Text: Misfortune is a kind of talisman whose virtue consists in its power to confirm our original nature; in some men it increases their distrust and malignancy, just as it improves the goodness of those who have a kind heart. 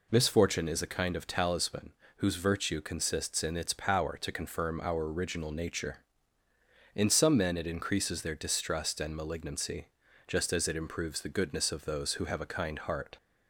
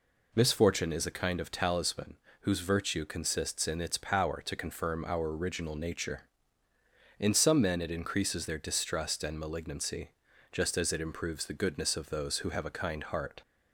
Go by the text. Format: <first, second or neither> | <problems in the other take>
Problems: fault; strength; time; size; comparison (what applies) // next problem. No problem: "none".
neither | pauses between "talisman" and "whose"; slight; the same in both